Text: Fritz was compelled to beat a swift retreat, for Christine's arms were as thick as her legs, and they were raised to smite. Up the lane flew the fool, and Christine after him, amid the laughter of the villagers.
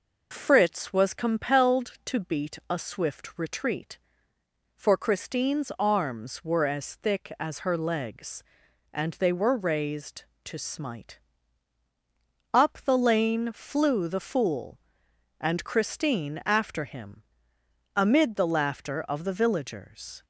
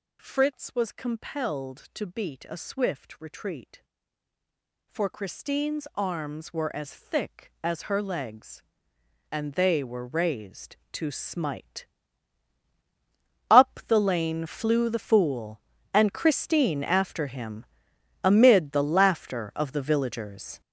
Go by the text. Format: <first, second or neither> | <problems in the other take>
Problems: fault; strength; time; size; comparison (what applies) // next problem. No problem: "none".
first | gets louder; strong; throughout; 11 dB